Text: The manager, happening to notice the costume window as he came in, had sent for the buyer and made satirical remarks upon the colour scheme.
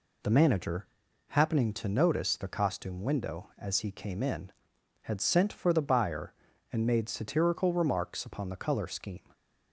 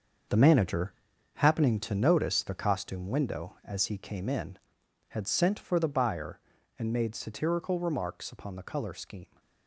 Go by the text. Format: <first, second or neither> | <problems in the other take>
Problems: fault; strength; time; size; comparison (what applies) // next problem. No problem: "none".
first | gets quieter; strong; throughout; 11 dB